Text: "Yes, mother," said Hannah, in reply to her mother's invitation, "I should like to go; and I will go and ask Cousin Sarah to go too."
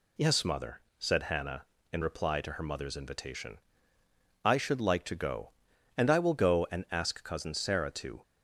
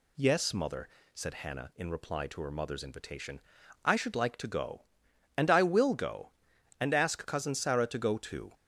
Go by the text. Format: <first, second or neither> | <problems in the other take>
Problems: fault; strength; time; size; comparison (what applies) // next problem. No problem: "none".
second | stops before "go too"; at 8.2 s